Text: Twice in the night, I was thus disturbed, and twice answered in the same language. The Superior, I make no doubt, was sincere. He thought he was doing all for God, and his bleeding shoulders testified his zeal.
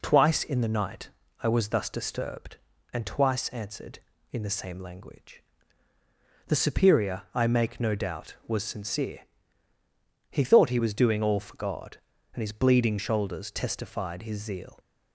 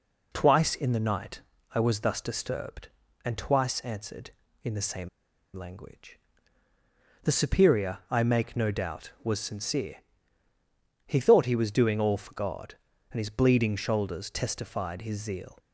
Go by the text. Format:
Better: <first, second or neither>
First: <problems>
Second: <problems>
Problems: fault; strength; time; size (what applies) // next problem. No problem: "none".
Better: first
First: none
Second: pauses between "same" and "language"; noticeable; at 5.0 s; 0.47 s long